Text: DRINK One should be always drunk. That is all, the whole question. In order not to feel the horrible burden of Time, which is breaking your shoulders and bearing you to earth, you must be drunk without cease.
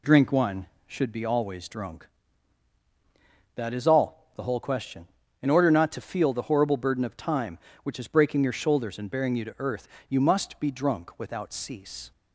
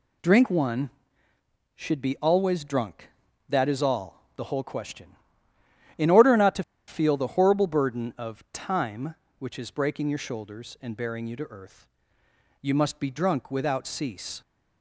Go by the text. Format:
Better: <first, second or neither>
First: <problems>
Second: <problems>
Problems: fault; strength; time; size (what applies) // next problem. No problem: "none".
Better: first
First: none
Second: pauses between "to" and "feel"; slight; at 6.6 s; 0.24 s long